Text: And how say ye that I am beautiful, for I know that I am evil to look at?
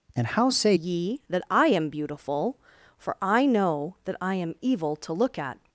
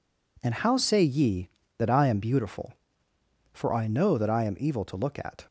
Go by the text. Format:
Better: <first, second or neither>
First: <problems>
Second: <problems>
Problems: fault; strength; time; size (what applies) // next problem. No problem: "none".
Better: second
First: changes voice at "ye"; from 0.7 s on; 4.9 s long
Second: none